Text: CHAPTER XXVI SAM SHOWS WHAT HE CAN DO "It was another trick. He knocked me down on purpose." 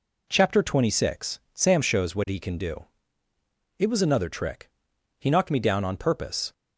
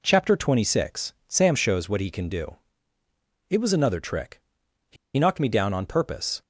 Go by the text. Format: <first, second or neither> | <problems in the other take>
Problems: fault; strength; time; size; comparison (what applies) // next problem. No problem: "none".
first | pauses between "DO" and "It"; noticeable; at 2.5 s; 0.96 s long; noticeable in the first // pauses between "He" and "knocked"; slight; at 4.9 s; 0.21 s long